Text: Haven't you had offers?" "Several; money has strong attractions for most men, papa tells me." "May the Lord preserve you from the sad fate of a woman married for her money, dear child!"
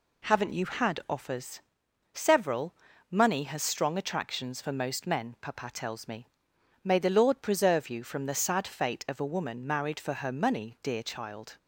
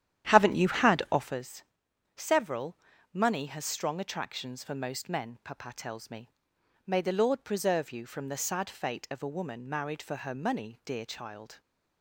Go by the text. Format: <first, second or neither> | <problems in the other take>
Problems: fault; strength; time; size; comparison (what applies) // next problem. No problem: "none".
first | starts louder than the rest; strong; until 1.4 s; 10.5 dB